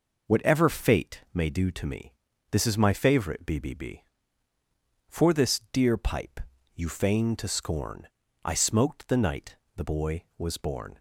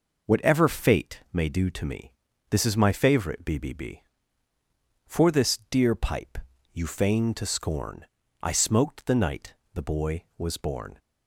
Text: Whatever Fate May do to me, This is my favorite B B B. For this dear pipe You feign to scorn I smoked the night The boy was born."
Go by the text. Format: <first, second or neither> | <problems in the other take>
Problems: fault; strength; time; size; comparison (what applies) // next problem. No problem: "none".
neither | pauses between "pipe" and "You"; slight; the same in both // pauses between "scorn" and "I"; slight; the same in both // pauses between "night" and "The"; slight; the same in both